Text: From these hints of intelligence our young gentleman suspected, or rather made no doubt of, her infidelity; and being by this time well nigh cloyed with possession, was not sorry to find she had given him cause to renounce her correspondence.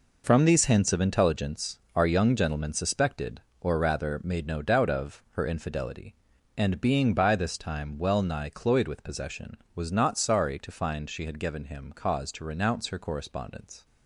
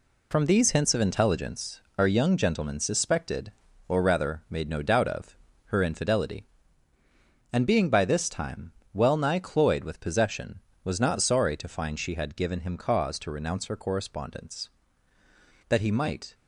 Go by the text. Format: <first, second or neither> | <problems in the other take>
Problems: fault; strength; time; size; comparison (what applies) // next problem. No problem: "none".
first | pauses between "intelligence" and "our"; slight; at 1.8 s; 0.16 s long; slight in the first // pauses between "time" and "well"; slight; at 8.7 s; 0.22 s long // goes on to say "That he might"; noticeable; from 15.6 s on; 0.66 s long